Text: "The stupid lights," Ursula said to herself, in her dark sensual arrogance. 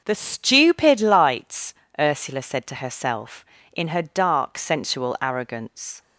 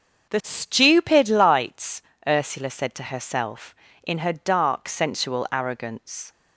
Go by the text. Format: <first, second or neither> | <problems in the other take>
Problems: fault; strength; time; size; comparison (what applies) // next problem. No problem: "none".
neither | starts louder than the rest; the same in both